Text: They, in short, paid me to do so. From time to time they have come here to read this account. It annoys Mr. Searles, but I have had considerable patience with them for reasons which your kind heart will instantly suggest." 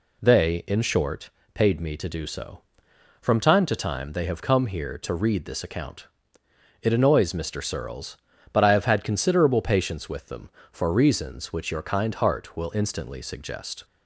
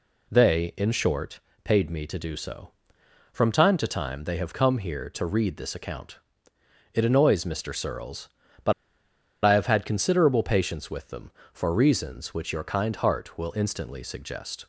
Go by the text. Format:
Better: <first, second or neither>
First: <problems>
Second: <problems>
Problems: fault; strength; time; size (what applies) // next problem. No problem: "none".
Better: first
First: none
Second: pauses between "but" and "I"; noticeable; at 8.7 s; 0.71 s long